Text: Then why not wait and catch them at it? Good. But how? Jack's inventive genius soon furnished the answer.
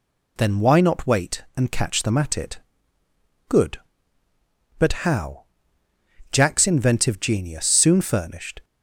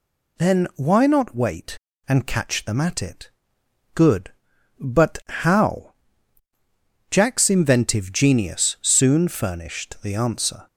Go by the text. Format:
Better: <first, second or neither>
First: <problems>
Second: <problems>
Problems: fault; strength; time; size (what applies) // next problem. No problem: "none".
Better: second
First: stops before "the answer"; at 8.6 s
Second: none